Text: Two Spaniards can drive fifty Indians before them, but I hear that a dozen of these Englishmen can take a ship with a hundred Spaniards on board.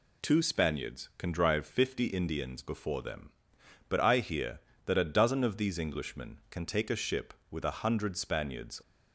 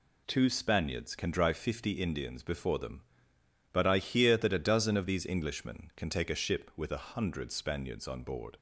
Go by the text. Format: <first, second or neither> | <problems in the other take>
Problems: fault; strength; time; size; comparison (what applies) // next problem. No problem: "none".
second | stops before "on board"; at 8.8 s